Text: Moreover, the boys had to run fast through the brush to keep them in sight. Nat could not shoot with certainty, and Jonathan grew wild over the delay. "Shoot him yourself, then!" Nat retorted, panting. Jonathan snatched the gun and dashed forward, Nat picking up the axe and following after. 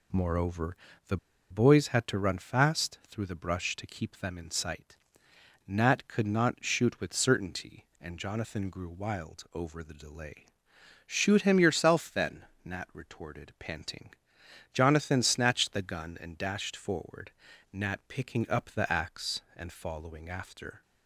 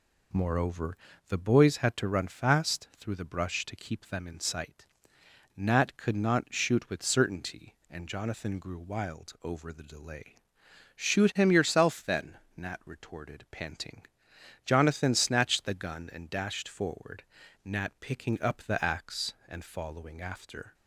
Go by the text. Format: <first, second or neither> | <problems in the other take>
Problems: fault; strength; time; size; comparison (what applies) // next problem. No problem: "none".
second | pauses between "the" and "boys"; slight; at 1.1 s; 0.34 s long